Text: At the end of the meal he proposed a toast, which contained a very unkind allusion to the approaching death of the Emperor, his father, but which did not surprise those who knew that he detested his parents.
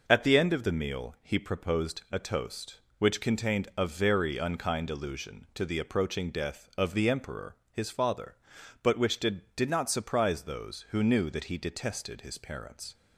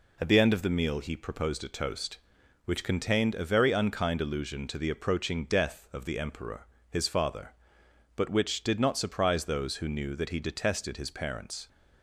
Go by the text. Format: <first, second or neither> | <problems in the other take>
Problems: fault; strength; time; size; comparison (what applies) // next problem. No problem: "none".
second | says "did" twice; at 9.5 s